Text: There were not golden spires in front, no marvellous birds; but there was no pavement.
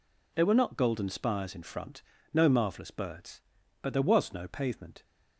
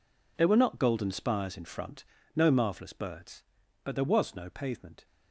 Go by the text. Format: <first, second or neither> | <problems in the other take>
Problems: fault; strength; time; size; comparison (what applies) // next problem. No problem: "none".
first | gets quieter; strong; throughout; 15 dB